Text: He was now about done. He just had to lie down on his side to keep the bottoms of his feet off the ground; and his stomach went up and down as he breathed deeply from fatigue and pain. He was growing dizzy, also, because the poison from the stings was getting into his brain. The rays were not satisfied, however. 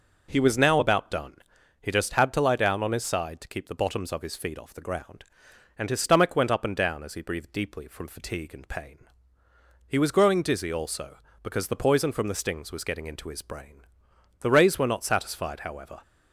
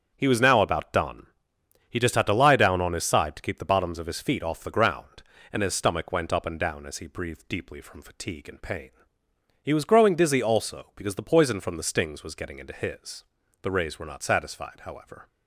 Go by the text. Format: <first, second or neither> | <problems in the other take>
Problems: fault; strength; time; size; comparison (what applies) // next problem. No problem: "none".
first | starts louder than the rest; strong; until 1.1 s; 8 dB // skips "brain"; at 13.4 s